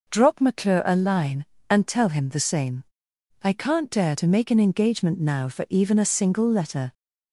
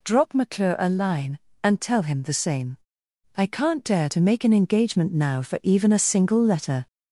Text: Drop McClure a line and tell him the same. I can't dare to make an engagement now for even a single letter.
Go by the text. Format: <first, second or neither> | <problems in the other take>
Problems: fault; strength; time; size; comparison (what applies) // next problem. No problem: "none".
first | gets louder; noticeable; throughout; 5 dB